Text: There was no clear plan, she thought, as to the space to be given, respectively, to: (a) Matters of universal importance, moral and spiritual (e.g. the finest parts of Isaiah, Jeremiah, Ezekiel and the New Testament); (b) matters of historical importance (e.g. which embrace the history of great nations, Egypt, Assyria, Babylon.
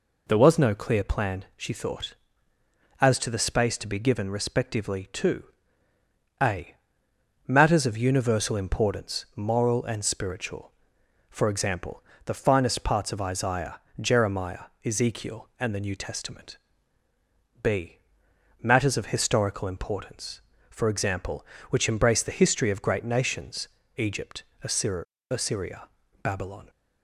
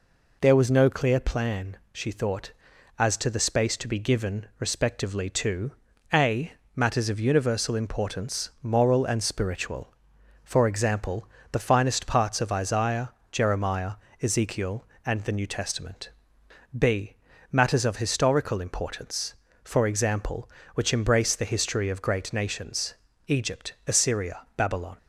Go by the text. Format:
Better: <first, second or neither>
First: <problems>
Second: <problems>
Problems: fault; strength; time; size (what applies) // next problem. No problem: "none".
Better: second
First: says "Assyria" twice; at 25.2 s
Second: none